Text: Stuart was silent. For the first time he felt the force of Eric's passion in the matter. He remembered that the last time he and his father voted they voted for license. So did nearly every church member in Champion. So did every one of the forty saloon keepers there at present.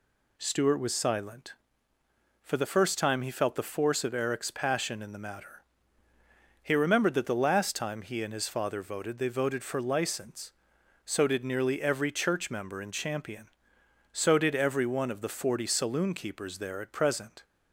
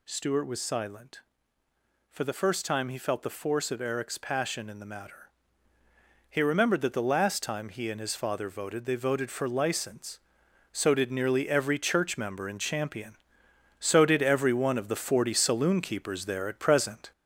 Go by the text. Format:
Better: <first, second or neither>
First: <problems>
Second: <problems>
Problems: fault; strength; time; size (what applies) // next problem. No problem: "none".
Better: first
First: none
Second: gets louder; noticeable; throughout; 5 dB